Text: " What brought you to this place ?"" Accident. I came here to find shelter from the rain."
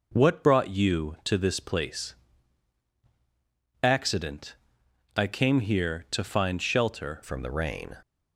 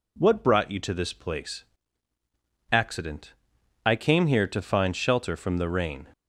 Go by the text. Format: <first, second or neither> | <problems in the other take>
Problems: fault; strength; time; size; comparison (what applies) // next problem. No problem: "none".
second | changes voice at "from"; from 7.2 s on; 0.7 s long